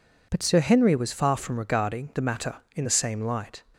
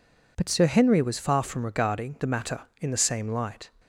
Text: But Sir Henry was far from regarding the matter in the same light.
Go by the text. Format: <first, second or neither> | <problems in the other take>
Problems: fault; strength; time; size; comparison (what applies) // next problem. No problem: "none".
neither | none